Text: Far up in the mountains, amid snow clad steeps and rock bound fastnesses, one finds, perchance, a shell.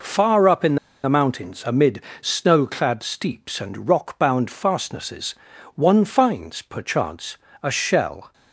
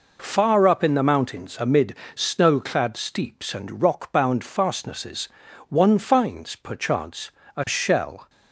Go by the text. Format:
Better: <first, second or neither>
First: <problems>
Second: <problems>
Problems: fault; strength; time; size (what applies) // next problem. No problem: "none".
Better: second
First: pauses between "in" and "the"; slight; at 0.7 s; 0.28 s long // pauses between "amid" and "snow"; slight; at 2.0 s; 0.18 s long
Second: pauses between "amid" and "snow"; slight; at 1.9 s; 0.18 s long